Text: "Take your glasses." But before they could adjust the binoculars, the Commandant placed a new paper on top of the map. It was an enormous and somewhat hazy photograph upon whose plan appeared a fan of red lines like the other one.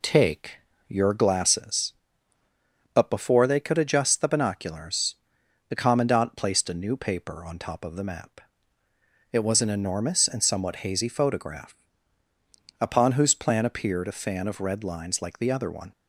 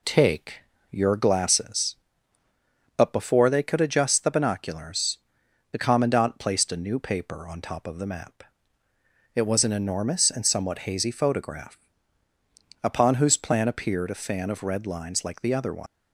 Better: first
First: pauses between "Take" and "your"; slight; at 0.5 s; 0.30 s long // pauses between "photograph" and "upon"; at 11.7 s; 1.0 s long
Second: pauses between "Take" and "your"; slight; at 0.6 s; 0.30 s long // pauses between "photograph" and "upon"; at 11.7 s; 1.0 s long // leaves "one" unfinished; at 15.8 s; 80 ms

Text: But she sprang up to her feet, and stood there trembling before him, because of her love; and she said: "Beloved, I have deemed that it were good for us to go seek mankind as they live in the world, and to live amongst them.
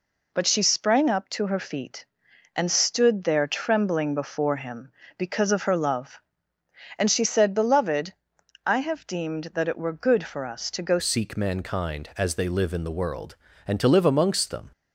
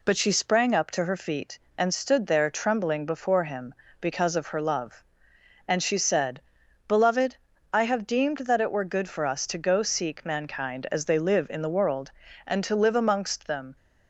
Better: second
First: changes voice at "seek"; from 10.9 s on; 3.7 s long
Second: none

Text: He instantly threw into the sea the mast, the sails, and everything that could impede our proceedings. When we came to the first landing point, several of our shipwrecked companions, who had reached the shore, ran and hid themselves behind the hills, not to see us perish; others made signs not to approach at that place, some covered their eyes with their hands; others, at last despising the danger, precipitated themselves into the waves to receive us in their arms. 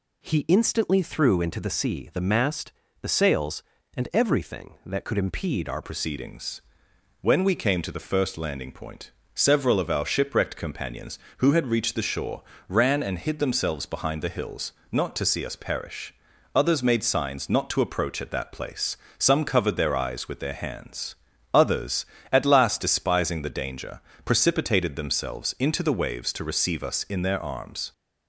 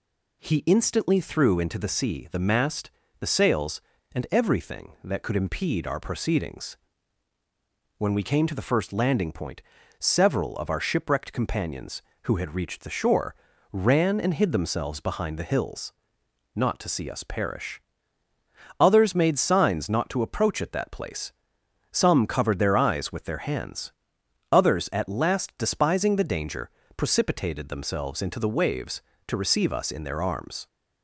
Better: second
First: changes voice at "proceedings"; from 5.8 s on; 22.1 s long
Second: none

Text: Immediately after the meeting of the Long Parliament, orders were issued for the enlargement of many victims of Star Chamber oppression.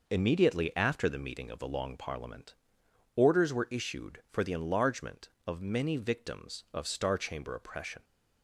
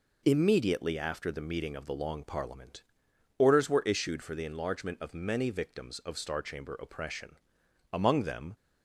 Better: first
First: none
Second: goes on to say "Among them"; noticeable; from 7.9 s on; 0.64 s long

